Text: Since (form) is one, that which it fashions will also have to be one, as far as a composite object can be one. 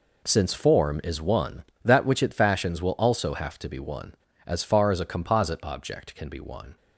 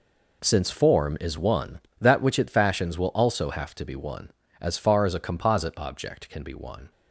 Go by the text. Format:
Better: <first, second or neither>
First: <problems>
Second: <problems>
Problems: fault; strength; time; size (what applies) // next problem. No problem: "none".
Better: neither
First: none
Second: none